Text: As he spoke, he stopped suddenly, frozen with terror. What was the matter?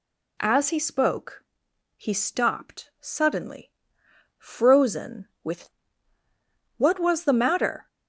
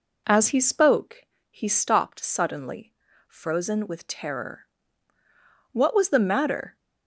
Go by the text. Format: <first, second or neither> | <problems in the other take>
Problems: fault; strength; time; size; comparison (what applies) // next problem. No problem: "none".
second | skips "terror"; at 6.2 s